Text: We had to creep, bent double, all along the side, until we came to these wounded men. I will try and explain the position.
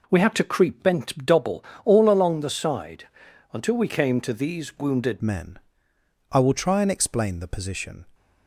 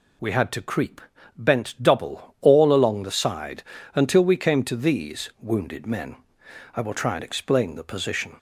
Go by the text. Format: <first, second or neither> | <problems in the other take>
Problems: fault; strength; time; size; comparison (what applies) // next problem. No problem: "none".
second | changes voice at "men"; from 5.2 s on; 2.8 s long